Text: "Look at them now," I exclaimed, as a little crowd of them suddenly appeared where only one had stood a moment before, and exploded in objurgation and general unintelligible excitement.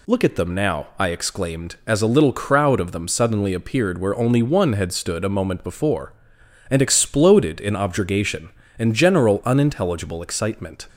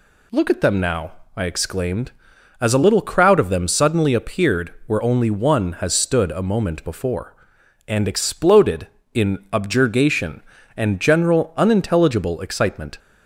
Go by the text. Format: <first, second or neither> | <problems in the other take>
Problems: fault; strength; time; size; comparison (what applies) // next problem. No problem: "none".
first | says "has" for "had"; at 5.7 s